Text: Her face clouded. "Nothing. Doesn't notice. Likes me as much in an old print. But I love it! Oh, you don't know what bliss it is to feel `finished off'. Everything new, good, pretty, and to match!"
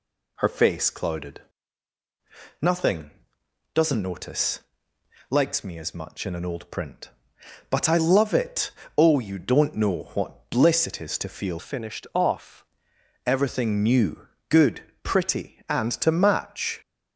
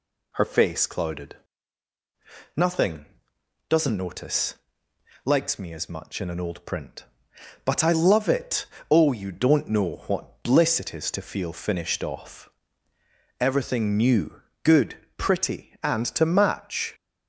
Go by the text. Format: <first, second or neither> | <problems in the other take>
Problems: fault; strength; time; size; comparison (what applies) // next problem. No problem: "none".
second | changes voice from "finished" to "off"; from 11.5 to 12.6 s; 1.1 s long